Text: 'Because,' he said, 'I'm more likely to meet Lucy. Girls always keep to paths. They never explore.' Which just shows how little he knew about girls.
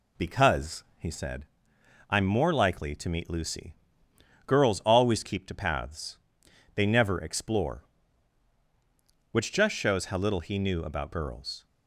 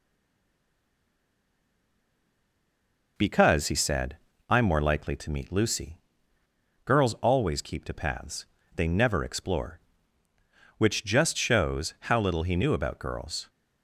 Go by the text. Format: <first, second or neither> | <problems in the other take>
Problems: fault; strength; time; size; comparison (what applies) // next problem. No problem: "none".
first | stays silent before the first word; strong; until 3.1 s; 3.1 s long